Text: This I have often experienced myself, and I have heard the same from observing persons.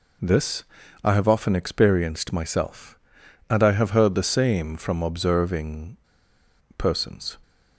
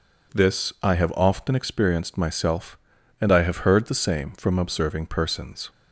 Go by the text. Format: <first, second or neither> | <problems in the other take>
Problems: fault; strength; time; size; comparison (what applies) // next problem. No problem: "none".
second | pauses between "This" and "I"; at 0.6 s; 0.40 s long // pauses between "observing" and "persons"; noticeable; at 5.9 s; 0.79 s long